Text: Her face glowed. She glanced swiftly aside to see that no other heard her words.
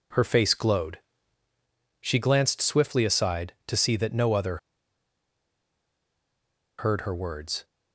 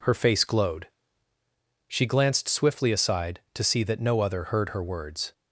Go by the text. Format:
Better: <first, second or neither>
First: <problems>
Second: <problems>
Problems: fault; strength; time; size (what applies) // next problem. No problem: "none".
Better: second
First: pauses between "other" and "heard"; strong; at 4.5 s; 2.2 s long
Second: none